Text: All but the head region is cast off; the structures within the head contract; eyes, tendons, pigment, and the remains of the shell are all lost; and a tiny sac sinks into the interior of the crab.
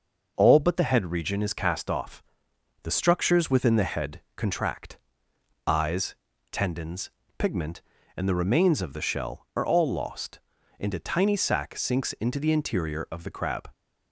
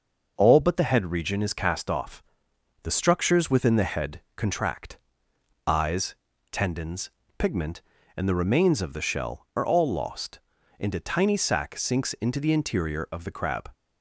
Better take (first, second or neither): neither